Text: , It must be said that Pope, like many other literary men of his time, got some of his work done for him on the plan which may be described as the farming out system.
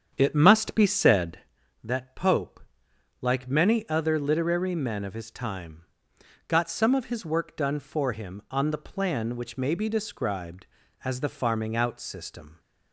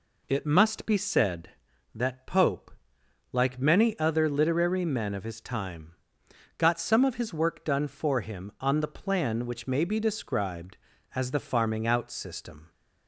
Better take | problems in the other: second | starts louder than the rest; strong; until 1.4 s; 8 dB

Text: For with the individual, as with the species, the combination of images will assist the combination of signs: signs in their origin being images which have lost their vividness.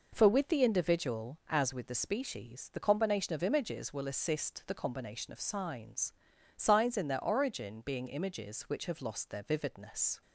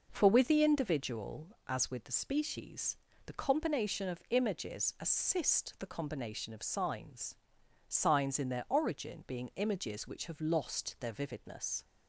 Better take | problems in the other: first | skips "will"; at 4.9 s

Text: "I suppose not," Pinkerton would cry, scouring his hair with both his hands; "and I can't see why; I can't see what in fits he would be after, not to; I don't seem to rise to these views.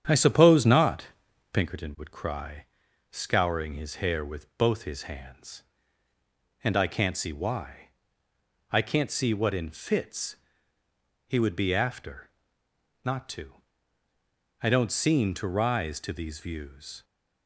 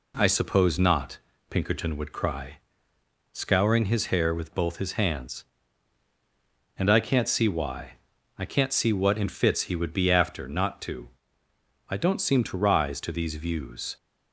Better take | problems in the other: second | starts louder than the rest; strong; until 1.7 s; 9 dB // pauses between "fits" and "he"; noticeable; at 10.3 s; 0.90 s long

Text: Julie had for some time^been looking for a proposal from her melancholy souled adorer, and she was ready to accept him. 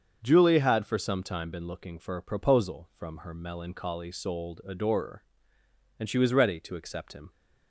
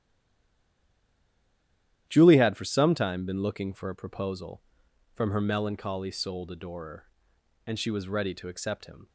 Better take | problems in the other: first | stays silent before the first word; noticeable; until 2.0 s; 2.0 s long // starts louder than the rest; strong; until 3.0 s; 12 dB; also in the first

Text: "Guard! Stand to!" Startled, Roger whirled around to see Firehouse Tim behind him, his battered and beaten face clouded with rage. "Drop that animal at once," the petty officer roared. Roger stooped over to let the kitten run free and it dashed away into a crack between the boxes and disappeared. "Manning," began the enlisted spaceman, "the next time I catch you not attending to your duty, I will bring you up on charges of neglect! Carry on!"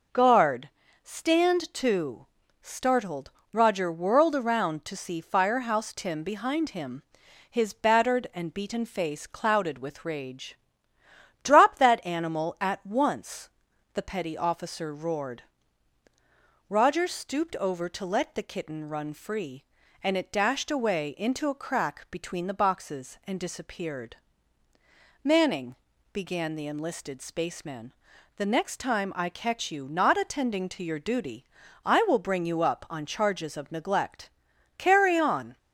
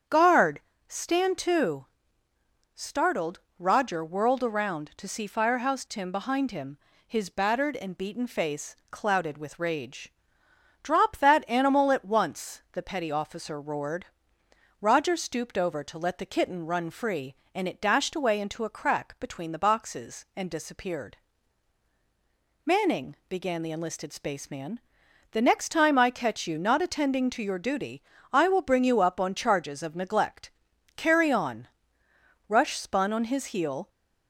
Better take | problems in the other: first | starts louder than the rest; strong; until 1.3 s; 8 dB // pauses between "face" and "clouded"; slight; at 8.7 s; 0.16 s long // goes on to say "Rush spun on his heel"; from 32.4 s on; 1.4 s long

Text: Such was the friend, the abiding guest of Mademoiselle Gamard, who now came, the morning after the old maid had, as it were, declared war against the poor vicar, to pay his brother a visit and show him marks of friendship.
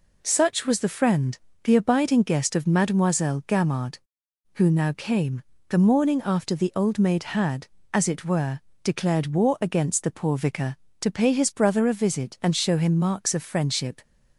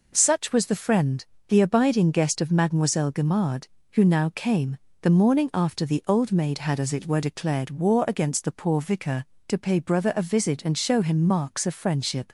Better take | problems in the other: first | skips "his"; at 9.7 s

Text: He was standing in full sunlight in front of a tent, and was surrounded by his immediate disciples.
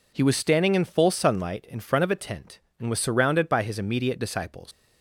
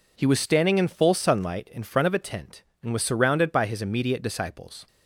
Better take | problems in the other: second | leaves "disciples" unfinished; at 4.7 s; 120 ms

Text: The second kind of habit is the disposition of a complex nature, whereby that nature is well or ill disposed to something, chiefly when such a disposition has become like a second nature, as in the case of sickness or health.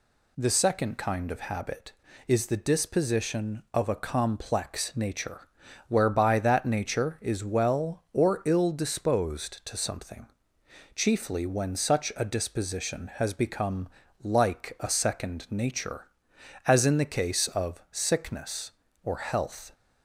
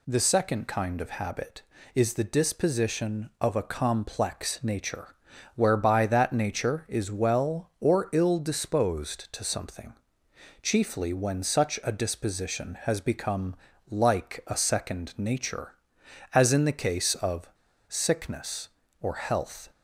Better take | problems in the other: first | pauses between "become" and "like"; slight; at 13.5 s; 0.36 s long; slight in the first // pauses between "of" and "sickness"; at 17.4 s; 0.40 s long

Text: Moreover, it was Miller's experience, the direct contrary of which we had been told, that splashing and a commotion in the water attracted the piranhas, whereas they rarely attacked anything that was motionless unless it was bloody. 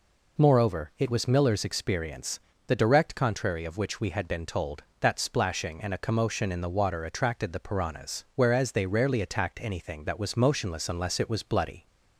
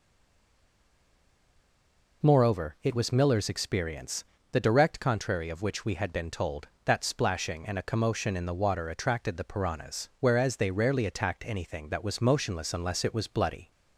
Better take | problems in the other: first | stays silent before the first word; until 2.2 s; 2.2 s long

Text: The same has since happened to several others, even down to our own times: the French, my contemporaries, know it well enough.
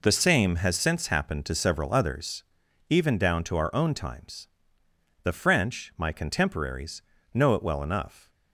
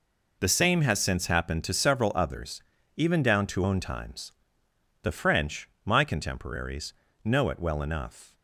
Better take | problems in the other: first | skips "our"; at 3.6 s

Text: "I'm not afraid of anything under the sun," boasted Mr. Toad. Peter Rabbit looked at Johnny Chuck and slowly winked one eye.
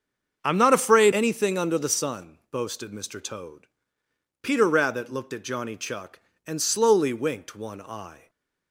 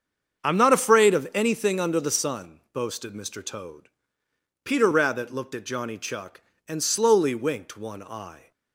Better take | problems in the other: second | starts louder than the rest; strong; until 1.4 s; 7 dB; strong in the second // skips "of"; at 1.1 s // stays silent after the last word; slight; from 8.1 s on; 0.6 s long

